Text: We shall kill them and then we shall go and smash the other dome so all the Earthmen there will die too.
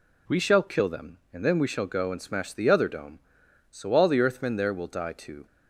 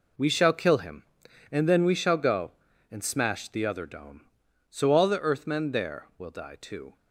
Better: first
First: none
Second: says "him" for "them"; at 0.7 s

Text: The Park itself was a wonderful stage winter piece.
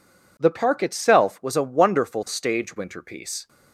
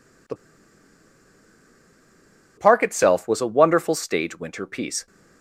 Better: first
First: none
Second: pauses between "The" and "Park"; strong; at 0.3 s; 2.2 s long

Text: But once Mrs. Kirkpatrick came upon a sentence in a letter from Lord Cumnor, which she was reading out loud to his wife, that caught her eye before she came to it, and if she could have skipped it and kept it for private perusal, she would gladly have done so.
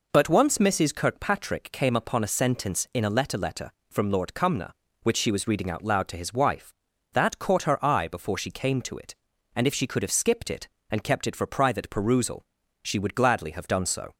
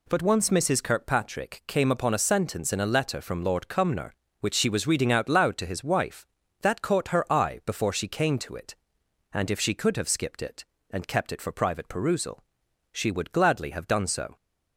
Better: second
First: says "letter" twice; at 3.3 s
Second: none

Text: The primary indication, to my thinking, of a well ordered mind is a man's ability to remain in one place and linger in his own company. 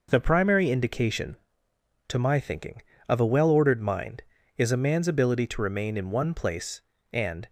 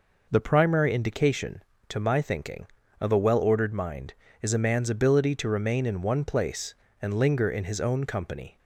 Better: second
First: stops before "linger in his own company"; at 7.4 s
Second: none

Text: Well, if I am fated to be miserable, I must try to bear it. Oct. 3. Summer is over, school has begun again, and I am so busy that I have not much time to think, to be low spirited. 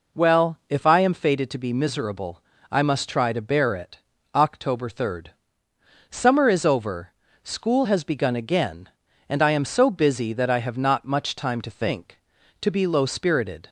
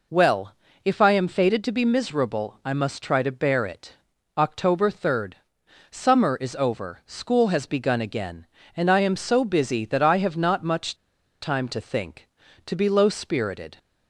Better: first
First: none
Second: pauses between "much" and "time"; noticeable; at 10.9 s; 0.47 s long

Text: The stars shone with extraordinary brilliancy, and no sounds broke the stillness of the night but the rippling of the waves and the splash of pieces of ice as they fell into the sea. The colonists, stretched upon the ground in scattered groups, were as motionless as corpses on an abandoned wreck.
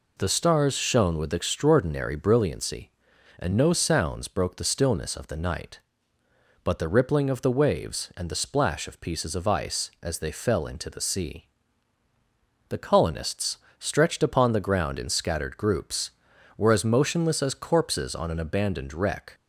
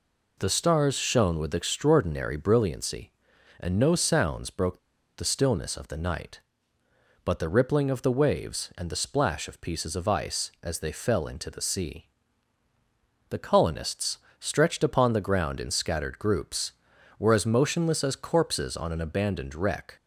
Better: first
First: none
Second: pauses between "broke" and "the"; at 4.7 s; 0.39 s long

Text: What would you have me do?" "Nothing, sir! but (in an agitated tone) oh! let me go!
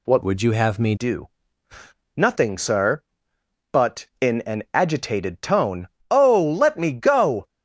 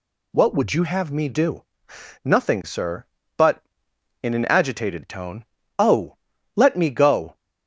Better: second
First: changes voice from "would" to "me"; from 0.2 to 0.9 s; 0.7 s long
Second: none

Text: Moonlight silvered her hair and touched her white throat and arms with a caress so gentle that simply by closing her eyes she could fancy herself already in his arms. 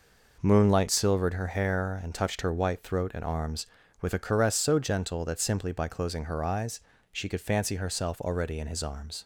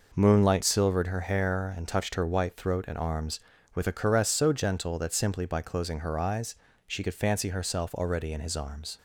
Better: neither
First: pauses between "eyes" and "she"; slight; at 6.7 s; 0.32 s long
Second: pauses between "eyes" and "she"; slight; at 6.5 s; 0.32 s long

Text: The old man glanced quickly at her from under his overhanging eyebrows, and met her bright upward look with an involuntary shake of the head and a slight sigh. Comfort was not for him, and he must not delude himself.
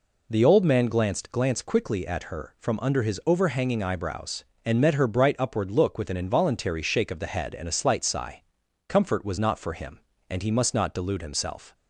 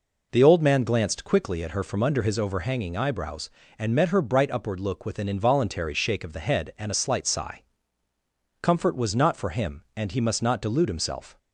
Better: second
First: says "glanced" twice; at 1.3 s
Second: none

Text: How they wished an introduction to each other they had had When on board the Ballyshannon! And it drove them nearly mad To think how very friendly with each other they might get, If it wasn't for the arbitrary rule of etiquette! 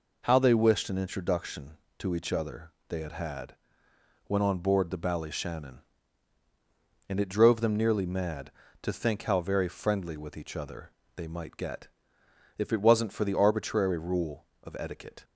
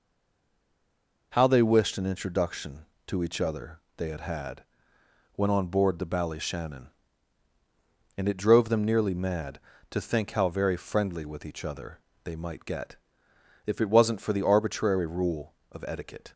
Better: first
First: pauses between "other" and "they"; slight; at 2.7 s; 0.18 s long // pauses between "had" and "When"; noticeable; at 3.5 s; 0.70 s long // pauses between "other" and "they"; slight; at 10.9 s; 0.24 s long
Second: stays silent before the first word; noticeable; until 1.3 s; 1.3 s long // pauses between "other" and "they"; slight; at 3.8 s; 0.18 s long // pauses between "had" and "When"; noticeable; at 4.6 s; 0.70 s long // pauses between "other" and "they"; slight; at 12.0 s; 0.24 s long

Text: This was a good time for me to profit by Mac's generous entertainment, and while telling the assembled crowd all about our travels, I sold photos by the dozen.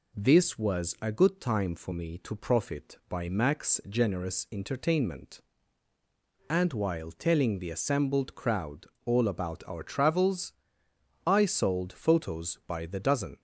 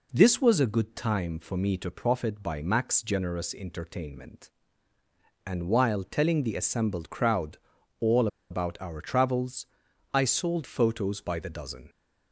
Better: first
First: pauses between "crowd" and "all"; slight; at 8.8 s; 0.18 s long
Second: pauses between "crowd" and "all"; at 7.5 s; 0.40 s long // pauses between "all" and "about"; slight; at 8.2 s; 0.23 s long

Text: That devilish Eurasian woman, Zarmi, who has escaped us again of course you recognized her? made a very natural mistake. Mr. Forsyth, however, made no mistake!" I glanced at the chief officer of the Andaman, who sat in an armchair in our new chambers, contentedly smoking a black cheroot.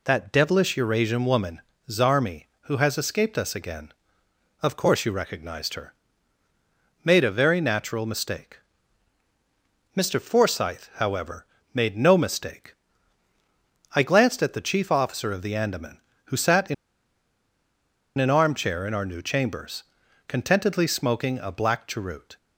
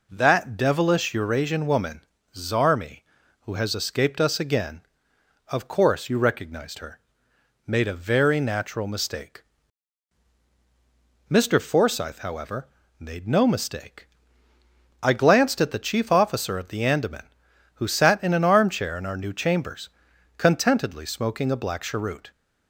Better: second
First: pauses between "in" and "an"; strong; at 16.7 s; 1.4 s long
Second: none

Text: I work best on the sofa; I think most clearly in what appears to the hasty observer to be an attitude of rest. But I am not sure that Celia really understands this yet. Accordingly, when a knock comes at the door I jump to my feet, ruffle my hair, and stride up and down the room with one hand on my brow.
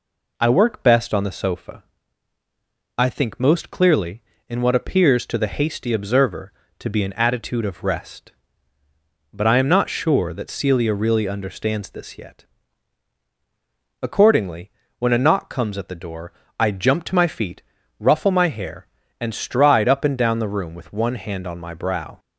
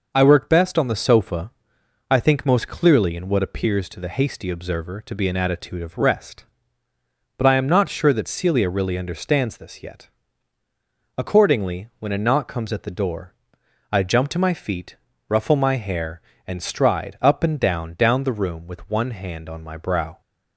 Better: first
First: pauses between "door" and "I"; slight; at 16.3 s; 0.26 s long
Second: pauses between "door" and "I"; noticeable; at 13.3 s; 0.58 s long // says "down" twice; at 17.9 s

